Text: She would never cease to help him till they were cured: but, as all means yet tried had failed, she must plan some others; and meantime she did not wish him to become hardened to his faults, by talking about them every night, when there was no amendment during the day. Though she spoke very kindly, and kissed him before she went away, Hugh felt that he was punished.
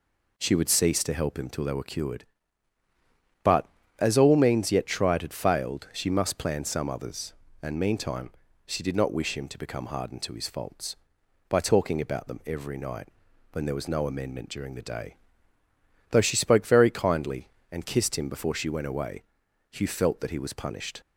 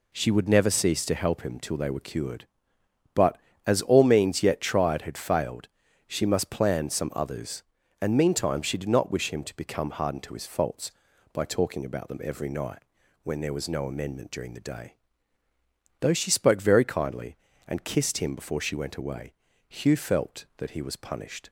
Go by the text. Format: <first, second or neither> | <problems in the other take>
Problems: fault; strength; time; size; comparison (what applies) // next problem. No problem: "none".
second | skips "never"; at 0.6 s // pauses between "meantime" and "she"; slight; at 8.3 s; 0.36 s long